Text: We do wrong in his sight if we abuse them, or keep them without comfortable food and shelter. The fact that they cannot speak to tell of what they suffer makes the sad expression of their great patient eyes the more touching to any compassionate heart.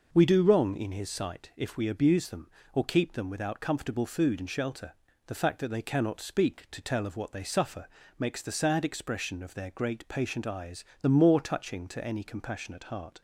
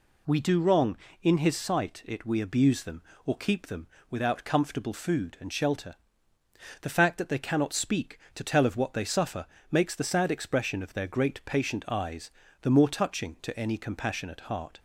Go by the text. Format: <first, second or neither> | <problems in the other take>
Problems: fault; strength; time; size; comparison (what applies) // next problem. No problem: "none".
first | says "it" for "if"; at 2.0 s // pauses between "them" and "without"; slight; at 3.8 s; 0.22 s long // pauses between "suffer" and "makes"; slight; at 9.4 s; 0.26 s long; slight in the first // pauses between "eyes" and "the"; slight; at 12.3 s; 0.32 s long; slight in the first